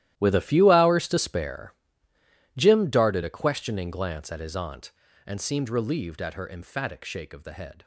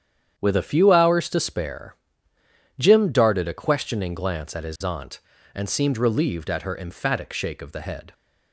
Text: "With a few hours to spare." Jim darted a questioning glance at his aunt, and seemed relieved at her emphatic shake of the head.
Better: second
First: gets quieter; strong; throughout; 16 dB // starts louder than the rest; strong; until 1.1 s; 13.5 dB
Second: starts louder than the rest; strong; until 1.3 s; 9 dB

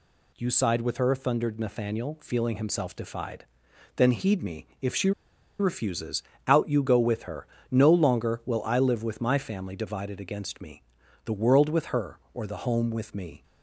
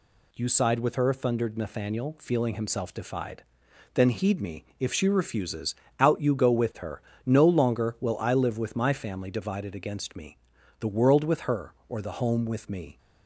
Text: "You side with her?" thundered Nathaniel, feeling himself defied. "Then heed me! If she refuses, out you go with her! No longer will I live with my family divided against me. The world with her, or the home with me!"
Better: second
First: pauses between "she" and "refuses"; noticeable; at 5.1 s; 0.48 s long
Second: none

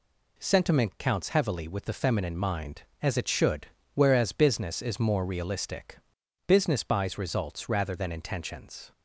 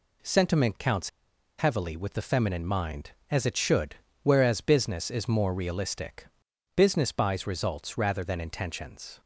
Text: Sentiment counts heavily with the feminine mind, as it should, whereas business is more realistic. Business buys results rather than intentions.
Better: first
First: none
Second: pauses between "counts" and "heavily"; noticeable; at 1.0 s; 0.48 s long

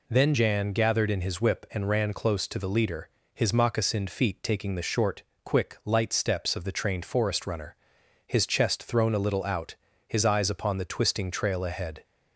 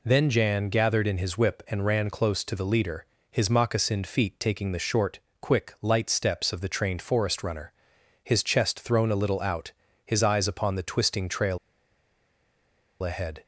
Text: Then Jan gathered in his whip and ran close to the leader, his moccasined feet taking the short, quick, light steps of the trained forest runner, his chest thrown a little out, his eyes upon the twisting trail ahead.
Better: first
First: none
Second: pauses between "trail" and "ahead"; strong; at 11.5 s; 1.4 s long

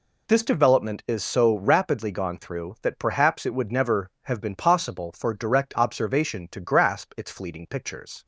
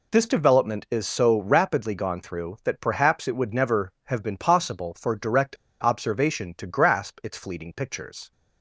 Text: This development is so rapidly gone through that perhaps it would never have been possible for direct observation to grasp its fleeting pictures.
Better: first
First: none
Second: pauses between "direct" and "observation"; slight; at 5.5 s; 0.27 s long

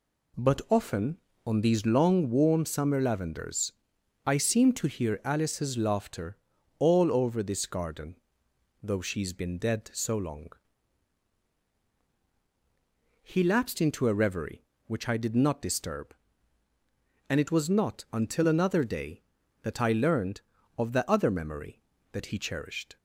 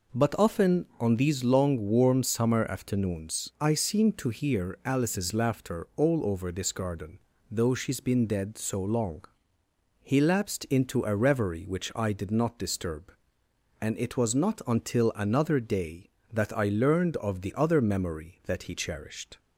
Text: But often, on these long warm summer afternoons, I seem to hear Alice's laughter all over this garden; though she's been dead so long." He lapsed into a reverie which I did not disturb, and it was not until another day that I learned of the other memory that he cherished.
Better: second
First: says "lavenders" for "afternoons"; at 3.0 s // pauses between "laughter" and "all"; at 6.3 s; 0.42 s long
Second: none

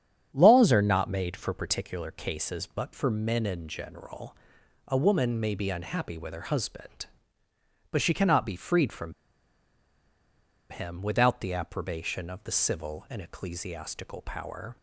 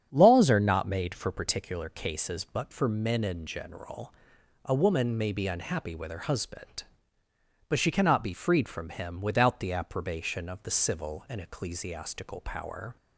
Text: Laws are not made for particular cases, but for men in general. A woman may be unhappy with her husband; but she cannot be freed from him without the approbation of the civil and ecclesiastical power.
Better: second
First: starts louder than the rest; strong; until 1.3 s; 8 dB // pauses between "from" and "him"; strong; at 9.1 s; 1.5 s long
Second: starts louder than the rest; strong; until 1.1 s; 8 dB

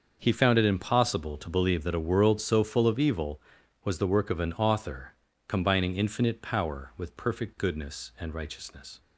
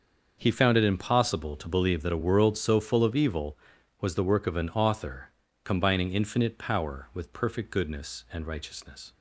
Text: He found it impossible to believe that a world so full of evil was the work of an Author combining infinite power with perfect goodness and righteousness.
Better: neither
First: starts louder than the rest; until 1.2 s; 6.5 dB // pauses between "Author" and "combining"; slight; at 5.1 s; 0.32 s long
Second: starts louder than the rest; until 1.4 s; 6.5 dB // pauses between "Author" and "combining"; slight; at 5.3 s; 0.32 s long

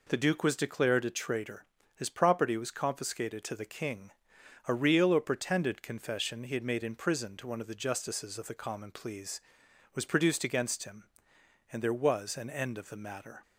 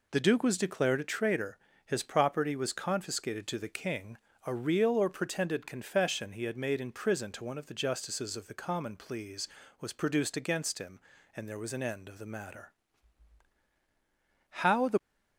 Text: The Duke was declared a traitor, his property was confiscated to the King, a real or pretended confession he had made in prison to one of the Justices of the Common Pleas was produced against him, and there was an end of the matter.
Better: first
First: none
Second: goes on to say "How the"; slight; from 14.5 s on; 0.44 s long

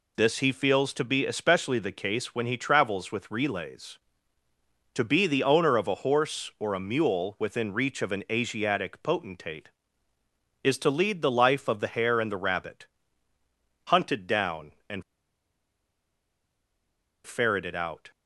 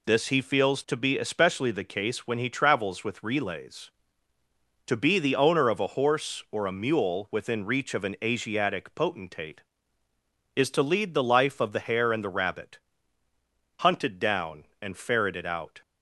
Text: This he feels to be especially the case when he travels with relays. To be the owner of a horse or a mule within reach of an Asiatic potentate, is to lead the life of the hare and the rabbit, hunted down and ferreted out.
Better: second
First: pauses between "and" and "ferreted"; strong; at 15.0 s; 2.2 s long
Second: none

